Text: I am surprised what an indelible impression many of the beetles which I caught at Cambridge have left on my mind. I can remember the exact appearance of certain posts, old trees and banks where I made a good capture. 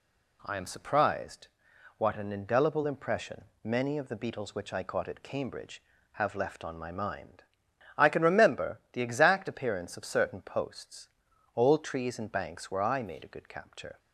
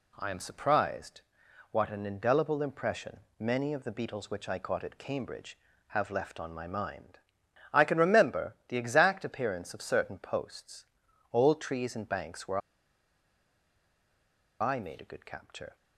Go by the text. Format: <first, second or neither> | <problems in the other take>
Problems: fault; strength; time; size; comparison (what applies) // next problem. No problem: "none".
first | pauses between "surprised" and "what"; noticeable; at 1.2 s; 0.50 s long; noticeable in the first // pauses between "impression" and "many"; slight; at 3.2 s; 0.18 s long; slight in the first // pauses between "where" and "I"; strong; at 12.5 s; 2.0 s long